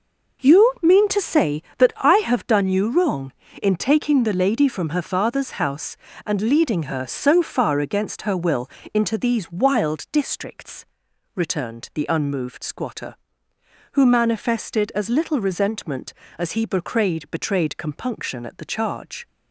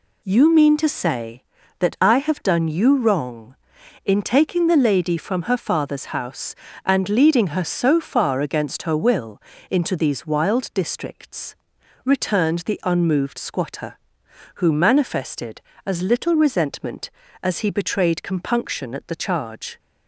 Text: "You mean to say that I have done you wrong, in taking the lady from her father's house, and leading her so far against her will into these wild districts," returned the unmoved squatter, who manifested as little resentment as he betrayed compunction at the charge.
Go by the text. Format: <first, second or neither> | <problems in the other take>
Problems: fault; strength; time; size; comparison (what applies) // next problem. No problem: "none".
second | pauses between "will" and "into"; slight; at 8.6 s; 0.24 s long; slight in the second // says "betrayed" twice; at 17.3 s